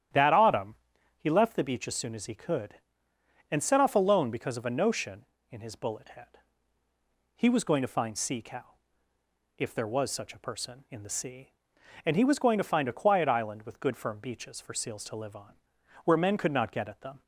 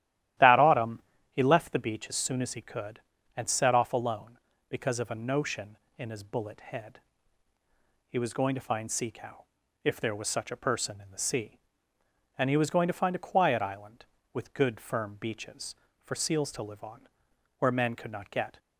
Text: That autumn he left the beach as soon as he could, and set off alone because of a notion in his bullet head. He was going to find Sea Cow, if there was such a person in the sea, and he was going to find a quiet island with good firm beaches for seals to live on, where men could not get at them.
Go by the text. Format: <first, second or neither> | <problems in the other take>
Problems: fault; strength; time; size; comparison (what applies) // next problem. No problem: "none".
first | starts louder than the rest; strong; until 1.7 s; 13 dB; strong in the first // pauses between "autumn" and "he"; slight; at 1.0 s; 0.32 s long; also in the first // stops before "at them"; at 18.5 s